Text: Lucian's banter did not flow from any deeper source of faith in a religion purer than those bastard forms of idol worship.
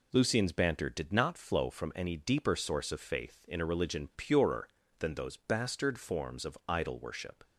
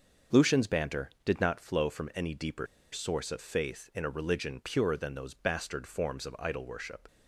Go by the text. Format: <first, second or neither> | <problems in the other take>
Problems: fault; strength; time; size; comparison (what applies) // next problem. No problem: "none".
first | starts louder than the rest; until 1.5 s; 6.5 dB // pauses between "deeper" and "source"; slight; at 2.6 s; 0.26 s long